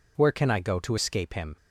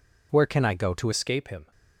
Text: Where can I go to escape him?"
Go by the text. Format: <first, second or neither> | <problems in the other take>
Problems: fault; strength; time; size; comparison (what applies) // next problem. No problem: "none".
first | changes voice at "escape"; from 1.1 s on; 0.6 s long